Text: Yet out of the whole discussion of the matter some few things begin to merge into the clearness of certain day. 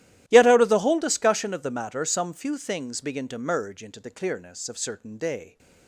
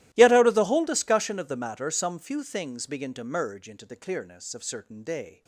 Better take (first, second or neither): first